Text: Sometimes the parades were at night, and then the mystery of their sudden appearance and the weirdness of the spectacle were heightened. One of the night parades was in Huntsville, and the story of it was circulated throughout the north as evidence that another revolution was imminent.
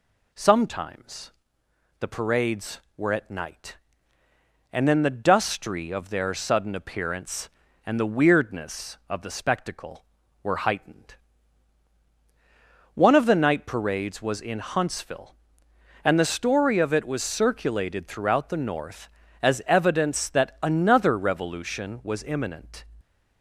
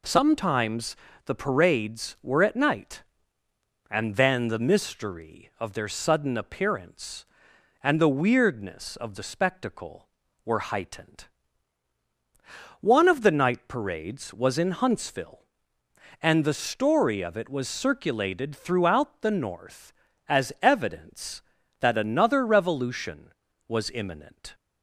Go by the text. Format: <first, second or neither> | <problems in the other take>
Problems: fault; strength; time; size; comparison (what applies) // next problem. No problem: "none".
second | pauses between "Sometimes" and "the"; noticeable; at 1.3 s; 0.70 s long; slight in the second // says "dustry" for "mystery"; at 5.1 s